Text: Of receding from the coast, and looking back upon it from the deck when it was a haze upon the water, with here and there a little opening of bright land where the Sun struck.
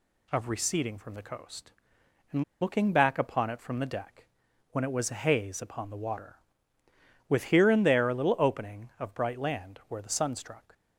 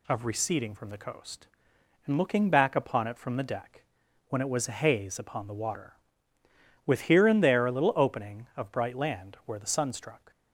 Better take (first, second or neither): second